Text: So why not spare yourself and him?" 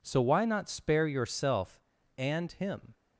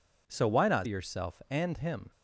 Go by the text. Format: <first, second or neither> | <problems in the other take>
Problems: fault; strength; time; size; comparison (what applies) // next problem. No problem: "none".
first | skips "spare"; at 0.8 s